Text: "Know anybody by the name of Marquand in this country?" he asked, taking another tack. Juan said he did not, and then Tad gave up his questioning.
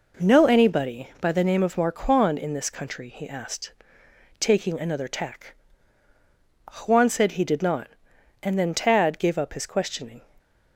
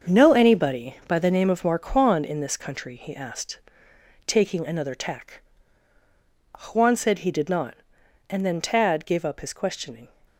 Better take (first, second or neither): first